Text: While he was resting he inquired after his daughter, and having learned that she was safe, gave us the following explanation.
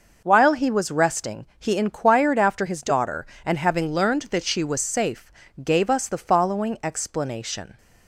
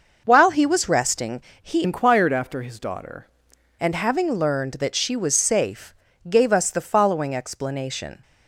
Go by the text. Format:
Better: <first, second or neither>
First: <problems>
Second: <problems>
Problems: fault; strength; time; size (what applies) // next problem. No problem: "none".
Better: first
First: pauses between "resting" and "he"; slight; at 1.4 s; 0.16 s long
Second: pauses between "resting" and "he"; slight; at 1.4 s; 0.20 s long // changes voice from "inquired" to "daughter"; from 1.8 to 3.2 s; 1.4 s long